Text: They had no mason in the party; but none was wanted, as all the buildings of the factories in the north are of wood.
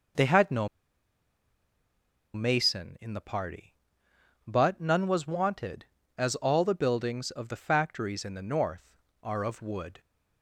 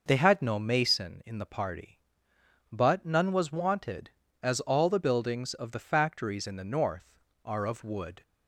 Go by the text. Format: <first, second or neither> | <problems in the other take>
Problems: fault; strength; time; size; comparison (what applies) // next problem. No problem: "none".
second | pauses between "no" and "mason"; strong; at 0.6 s; 1.6 s long